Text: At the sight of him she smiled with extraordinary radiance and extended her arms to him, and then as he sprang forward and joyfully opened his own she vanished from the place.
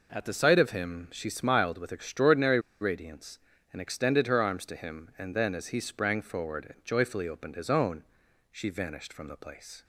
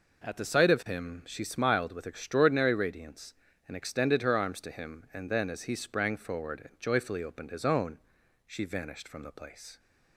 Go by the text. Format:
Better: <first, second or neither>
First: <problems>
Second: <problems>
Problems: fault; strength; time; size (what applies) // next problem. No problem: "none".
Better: second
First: pauses between "extraordinary" and "radiance"; slight; at 2.5 s; 0.22 s long // pauses between "own" and "she"; noticeable; at 8.0 s; 0.48 s long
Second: pauses between "own" and "she"; noticeable; at 7.9 s; 0.48 s long